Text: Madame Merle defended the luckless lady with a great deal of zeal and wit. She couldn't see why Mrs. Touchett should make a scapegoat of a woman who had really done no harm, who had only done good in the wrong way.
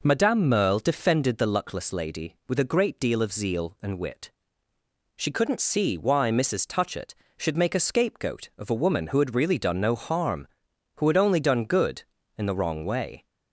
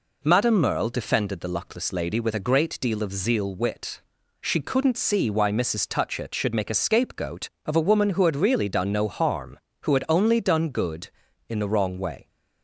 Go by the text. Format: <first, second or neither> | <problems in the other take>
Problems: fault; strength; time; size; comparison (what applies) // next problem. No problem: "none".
first | skips "and"; at 3.5 s